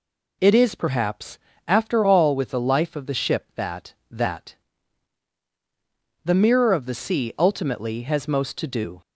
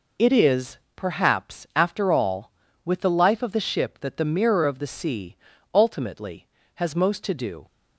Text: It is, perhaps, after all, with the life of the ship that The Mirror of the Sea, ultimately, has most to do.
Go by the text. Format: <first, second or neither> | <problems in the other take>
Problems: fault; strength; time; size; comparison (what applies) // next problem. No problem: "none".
second | says "that" twice; at 4.1 s